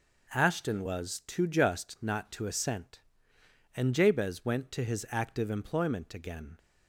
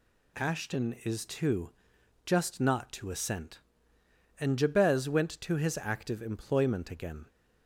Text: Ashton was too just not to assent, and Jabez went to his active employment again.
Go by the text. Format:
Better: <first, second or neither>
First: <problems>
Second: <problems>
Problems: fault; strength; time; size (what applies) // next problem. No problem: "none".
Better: first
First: none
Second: says "is" for "was"; at 1.0 s // pauses between "too" and "just"; noticeable; at 1.6 s; 0.56 s long